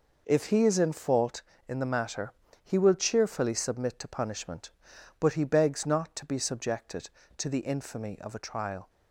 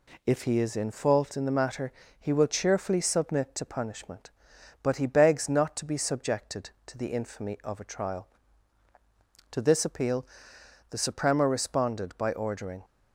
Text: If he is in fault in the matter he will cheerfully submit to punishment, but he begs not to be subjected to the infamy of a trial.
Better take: first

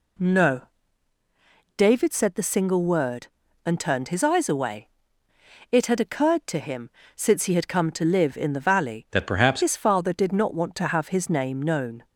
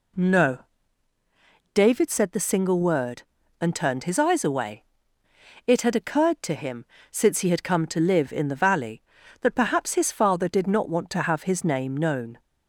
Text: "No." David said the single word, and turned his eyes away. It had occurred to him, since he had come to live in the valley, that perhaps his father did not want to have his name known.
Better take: second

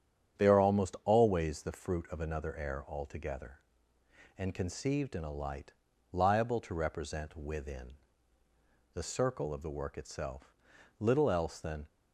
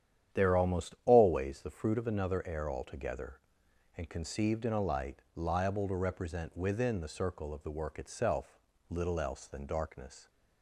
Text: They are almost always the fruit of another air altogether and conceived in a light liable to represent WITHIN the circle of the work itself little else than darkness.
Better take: second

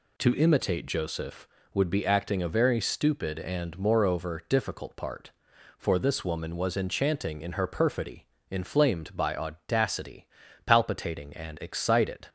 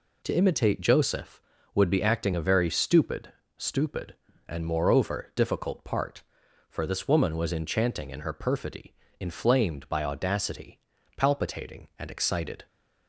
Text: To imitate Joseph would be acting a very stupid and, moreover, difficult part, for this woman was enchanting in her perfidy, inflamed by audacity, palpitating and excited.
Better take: first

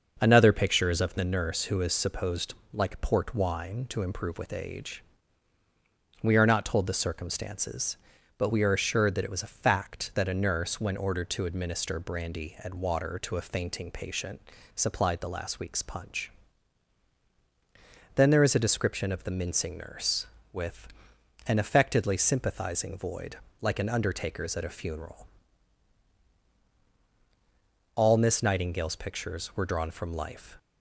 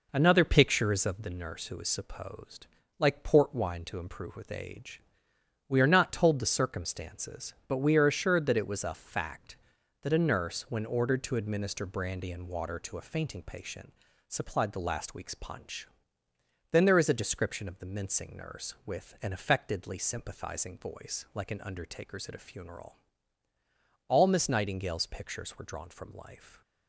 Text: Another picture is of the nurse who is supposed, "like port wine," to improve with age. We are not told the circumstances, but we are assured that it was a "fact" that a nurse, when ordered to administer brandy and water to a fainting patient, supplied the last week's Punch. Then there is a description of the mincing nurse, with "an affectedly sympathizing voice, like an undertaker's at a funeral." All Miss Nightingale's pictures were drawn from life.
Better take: second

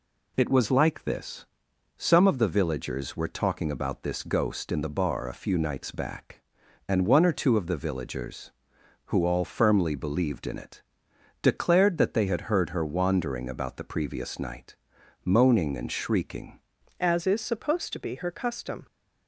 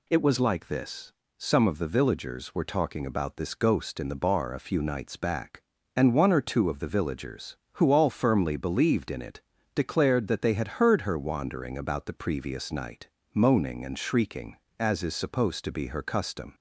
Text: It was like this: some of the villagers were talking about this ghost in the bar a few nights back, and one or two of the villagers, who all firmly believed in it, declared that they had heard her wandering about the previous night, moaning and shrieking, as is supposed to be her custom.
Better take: second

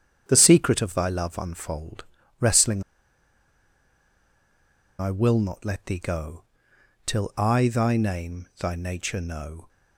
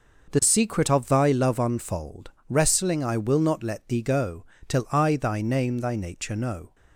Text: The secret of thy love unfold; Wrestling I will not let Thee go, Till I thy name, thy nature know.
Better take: second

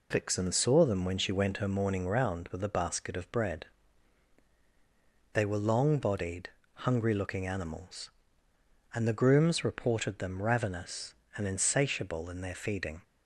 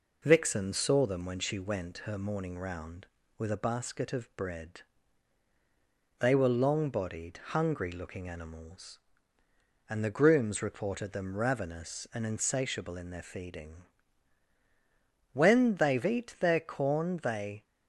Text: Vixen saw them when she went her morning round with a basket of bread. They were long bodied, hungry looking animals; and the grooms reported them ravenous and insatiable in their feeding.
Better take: first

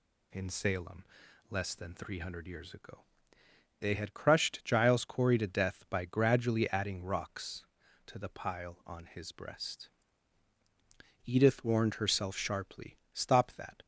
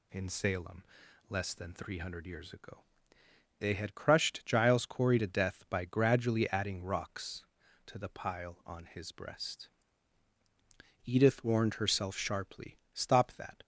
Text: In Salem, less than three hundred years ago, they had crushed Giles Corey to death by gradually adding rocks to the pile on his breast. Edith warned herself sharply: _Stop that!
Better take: neither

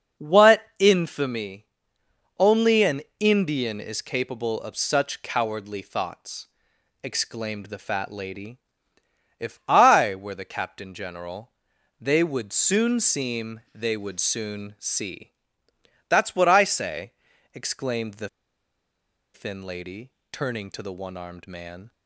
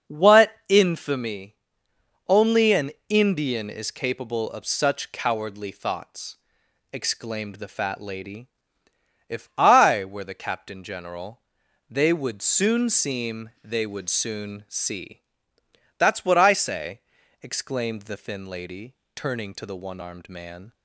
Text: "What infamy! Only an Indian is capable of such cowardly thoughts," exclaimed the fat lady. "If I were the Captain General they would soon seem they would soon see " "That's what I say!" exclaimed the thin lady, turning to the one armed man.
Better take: second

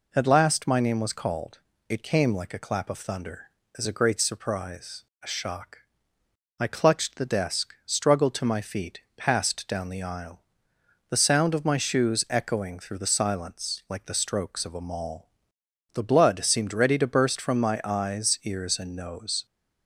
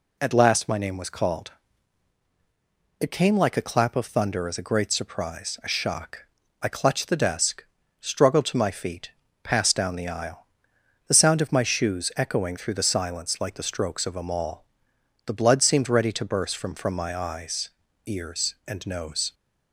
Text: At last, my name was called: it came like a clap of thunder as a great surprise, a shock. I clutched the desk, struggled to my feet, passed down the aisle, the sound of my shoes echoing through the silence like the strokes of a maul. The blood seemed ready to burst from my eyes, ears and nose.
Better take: first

